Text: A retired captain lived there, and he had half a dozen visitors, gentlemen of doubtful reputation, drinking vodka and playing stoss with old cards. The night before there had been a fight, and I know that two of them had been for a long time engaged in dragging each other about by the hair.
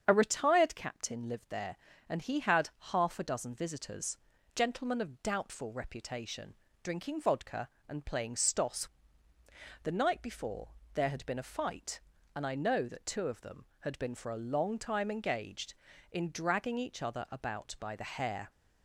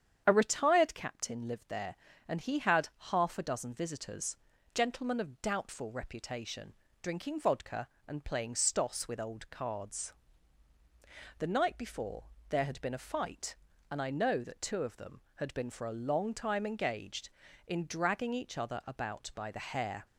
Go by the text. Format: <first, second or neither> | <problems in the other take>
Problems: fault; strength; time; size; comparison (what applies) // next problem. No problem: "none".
second | starts louder than the rest; strong; until 1.0 s; 8 dB; strong in the second // pauses between "had" and "half"; slight; at 2.6 s; 0.22 s long; slight in the second // skips "with old cards"; at 9.3 s // pauses between "before" and "there"; slight; at 10.7 s; 0.22 s long; slight in the second